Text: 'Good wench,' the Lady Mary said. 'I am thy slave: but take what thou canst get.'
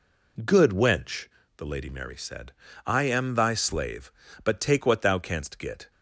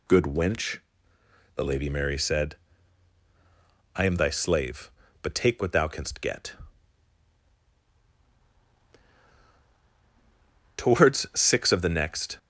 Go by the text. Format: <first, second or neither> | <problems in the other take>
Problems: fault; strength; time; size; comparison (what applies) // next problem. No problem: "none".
first | goes on to say "Towards six of the next"; from 10.7 s on; 1.6 s long